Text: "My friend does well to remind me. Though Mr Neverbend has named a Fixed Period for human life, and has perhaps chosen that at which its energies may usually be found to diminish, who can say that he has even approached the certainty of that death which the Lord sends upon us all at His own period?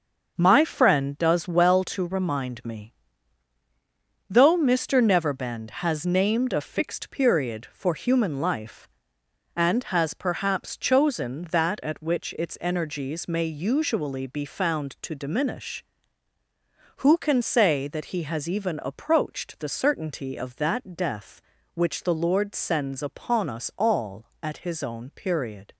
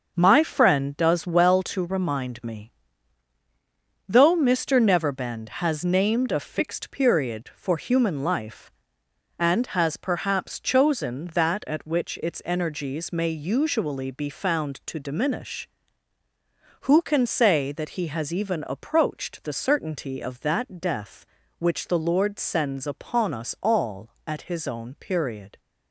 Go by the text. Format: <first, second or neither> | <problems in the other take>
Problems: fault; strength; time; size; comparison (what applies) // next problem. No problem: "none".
neither | starts louder than the rest; the same in both